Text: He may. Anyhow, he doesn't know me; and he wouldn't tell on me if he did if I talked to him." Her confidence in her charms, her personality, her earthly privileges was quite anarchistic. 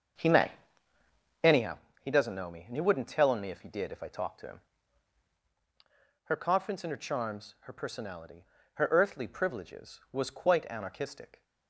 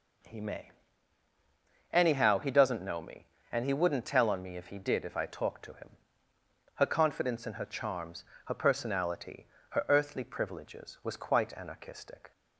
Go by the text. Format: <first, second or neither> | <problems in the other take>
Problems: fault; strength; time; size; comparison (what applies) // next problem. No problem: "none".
second | starts louder than the rest; until 1.7 s; 7 dB